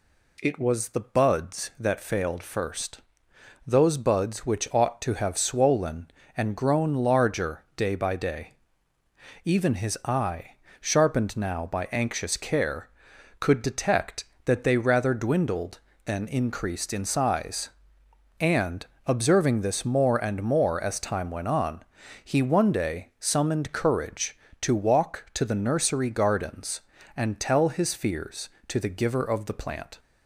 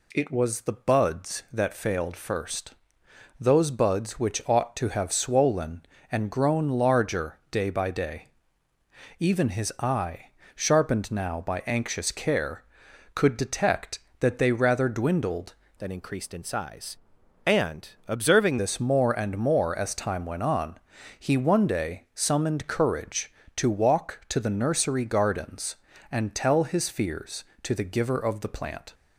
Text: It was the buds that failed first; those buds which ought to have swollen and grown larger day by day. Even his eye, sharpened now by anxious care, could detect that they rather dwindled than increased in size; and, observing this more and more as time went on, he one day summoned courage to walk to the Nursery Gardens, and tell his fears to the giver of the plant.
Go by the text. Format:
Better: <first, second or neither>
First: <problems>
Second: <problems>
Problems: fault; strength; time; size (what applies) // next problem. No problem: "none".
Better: first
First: none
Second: changes voice from "than" to "observing"; from 15.7 to 18.5 s; 2.8 s long